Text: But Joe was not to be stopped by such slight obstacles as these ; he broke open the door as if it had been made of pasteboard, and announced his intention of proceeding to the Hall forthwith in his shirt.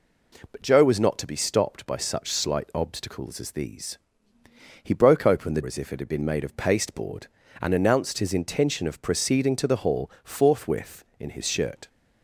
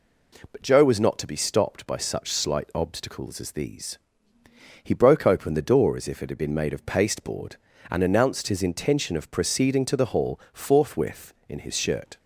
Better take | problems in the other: second | skips "door"; at 5.6 s

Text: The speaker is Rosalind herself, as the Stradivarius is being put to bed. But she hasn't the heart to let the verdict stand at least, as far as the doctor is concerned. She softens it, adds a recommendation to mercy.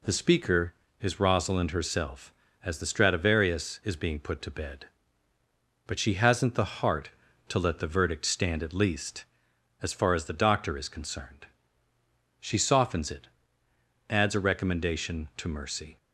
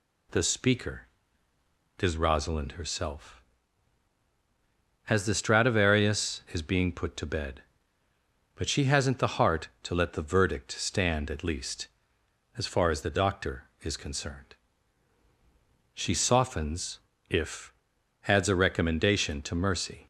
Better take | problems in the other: first | says "if" for "it"; at 17.2 s

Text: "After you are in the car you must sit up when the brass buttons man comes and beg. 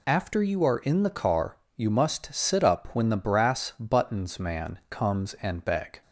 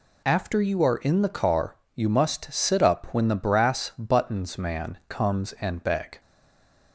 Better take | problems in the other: first | pauses between "car" and "you"; slight; at 1.7 s; 0.20 s long; slight in the first // stays silent after the last word; slight; from 6.1 s on; 0.8 s long

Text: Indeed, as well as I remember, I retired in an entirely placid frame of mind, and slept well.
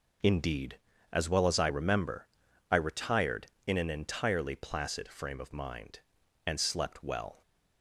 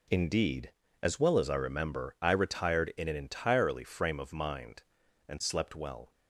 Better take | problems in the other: first | skips "placid"; at 3.8 s

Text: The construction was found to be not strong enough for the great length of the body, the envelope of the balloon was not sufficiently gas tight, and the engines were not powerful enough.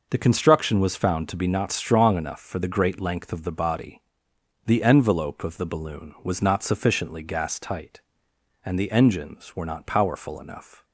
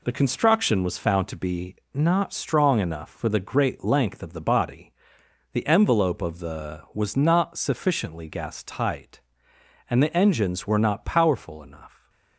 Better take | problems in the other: first | pauses between "be" and "not"; slight; at 1.7 s; 0.18 s long // skips "balloon"; at 6.8 s

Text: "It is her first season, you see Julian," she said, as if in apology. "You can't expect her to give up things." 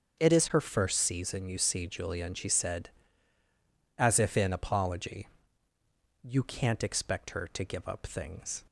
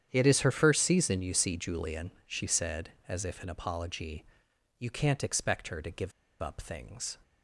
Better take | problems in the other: first | starts louder than the rest; strong; until 1.1 s; 9 dB; also in the first // pauses between "give" and "up"; slight; at 6.1 s; 0.31 s long

